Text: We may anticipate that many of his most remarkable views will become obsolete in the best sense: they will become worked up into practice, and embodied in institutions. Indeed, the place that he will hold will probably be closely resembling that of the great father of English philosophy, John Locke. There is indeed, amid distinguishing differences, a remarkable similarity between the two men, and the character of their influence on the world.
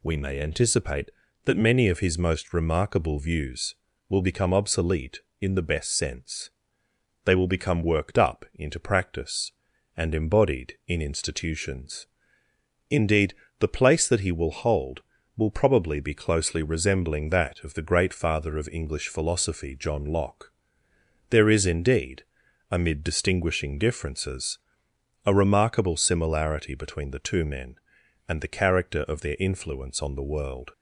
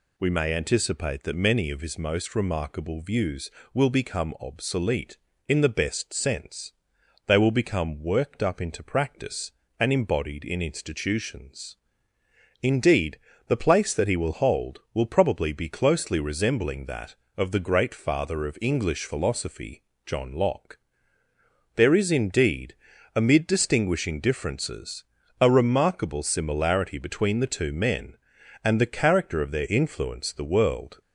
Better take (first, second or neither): first